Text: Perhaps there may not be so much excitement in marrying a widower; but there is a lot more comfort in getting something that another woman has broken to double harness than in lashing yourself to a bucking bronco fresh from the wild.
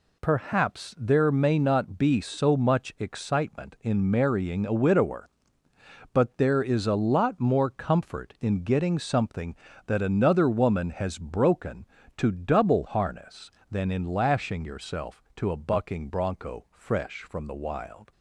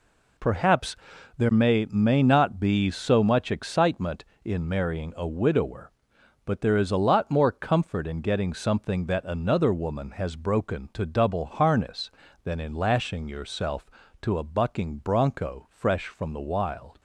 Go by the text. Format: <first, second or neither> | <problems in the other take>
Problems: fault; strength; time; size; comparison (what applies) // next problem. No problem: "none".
first | pauses between "Perhaps" and "there"; at 0.9 s; 0.42 s long // says "may" twice; at 1.8 s